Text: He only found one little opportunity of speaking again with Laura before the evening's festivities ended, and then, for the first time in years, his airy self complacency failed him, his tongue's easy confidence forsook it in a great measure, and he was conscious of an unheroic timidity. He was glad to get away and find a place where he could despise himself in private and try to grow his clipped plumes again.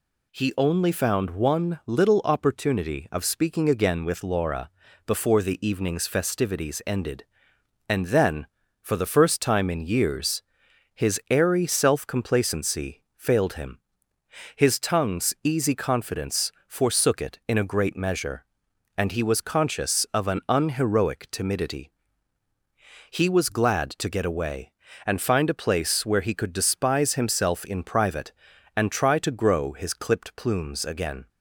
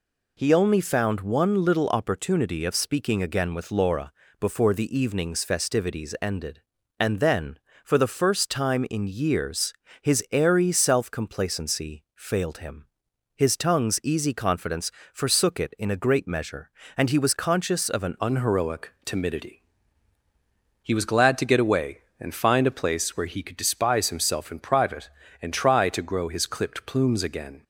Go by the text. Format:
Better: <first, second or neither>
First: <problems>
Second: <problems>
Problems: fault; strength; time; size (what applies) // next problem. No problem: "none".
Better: first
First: pauses between "Laura" and "before"; slight; at 4.6 s; 0.36 s long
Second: pauses between "Laura" and "before"; slight; at 4.1 s; 0.26 s long // pauses between "confidence" and "forsook"; slight; at 14.9 s; 0.20 s long // changes voice at "unheroic"; from 18.2 s on; 9.4 s long